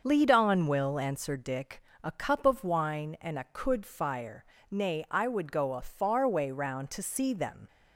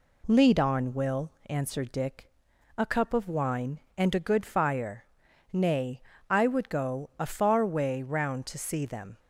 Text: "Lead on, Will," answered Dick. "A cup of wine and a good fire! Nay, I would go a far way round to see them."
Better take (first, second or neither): second